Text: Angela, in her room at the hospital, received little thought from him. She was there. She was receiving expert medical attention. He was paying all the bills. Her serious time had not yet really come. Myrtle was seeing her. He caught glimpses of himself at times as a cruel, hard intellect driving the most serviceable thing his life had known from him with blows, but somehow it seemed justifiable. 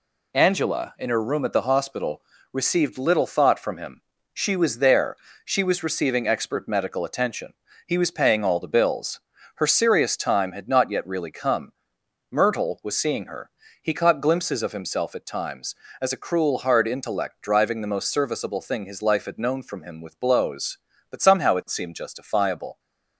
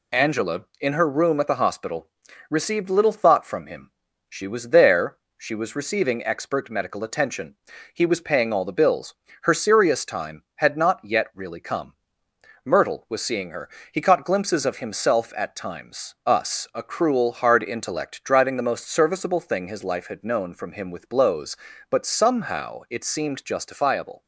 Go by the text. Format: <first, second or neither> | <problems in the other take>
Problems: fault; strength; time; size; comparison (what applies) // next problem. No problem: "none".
first | says "us" for "as"; at 16.2 s